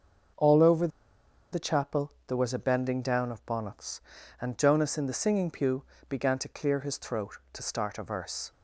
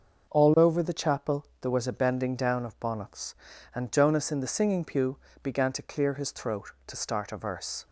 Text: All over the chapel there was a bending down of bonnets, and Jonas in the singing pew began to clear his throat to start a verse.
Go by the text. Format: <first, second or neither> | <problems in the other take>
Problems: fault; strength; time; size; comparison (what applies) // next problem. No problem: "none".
second | starts louder than the rest; until 2.0 s; 6.5 dB // pauses between "over" and "the"; noticeable; at 0.8 s; 0.64 s long // pauses between "pew" and "began"; slight; at 5.8 s; 0.24 s long; slight in the second